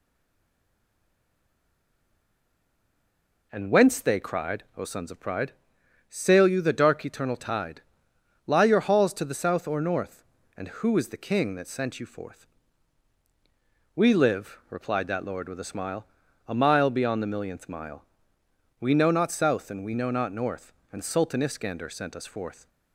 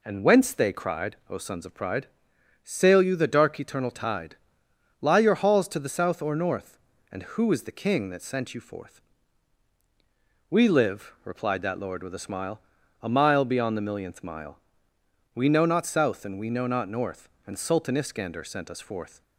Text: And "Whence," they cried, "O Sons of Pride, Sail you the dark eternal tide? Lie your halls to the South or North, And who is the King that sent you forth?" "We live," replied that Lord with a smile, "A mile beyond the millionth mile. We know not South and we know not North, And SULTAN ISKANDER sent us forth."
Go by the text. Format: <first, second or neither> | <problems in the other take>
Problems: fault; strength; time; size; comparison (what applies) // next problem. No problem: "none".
second | stays silent before the first word; strong; until 3.5 s; 3.5 s long